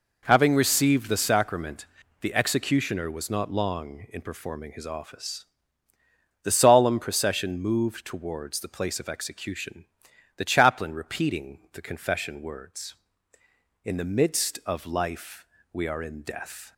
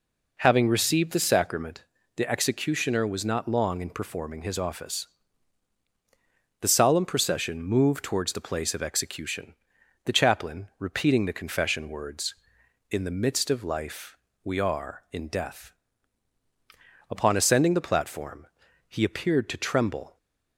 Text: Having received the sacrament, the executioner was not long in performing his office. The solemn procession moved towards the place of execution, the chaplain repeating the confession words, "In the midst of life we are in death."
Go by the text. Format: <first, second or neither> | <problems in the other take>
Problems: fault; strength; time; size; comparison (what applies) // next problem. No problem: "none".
first | pauses between "life" and "we"; slight; at 14.1 s; 0.28 s long; slight in the first // goes on to say "Upon ascending the platform he appeared to tremble"; strong; from 17.0 s on; 3.0 s long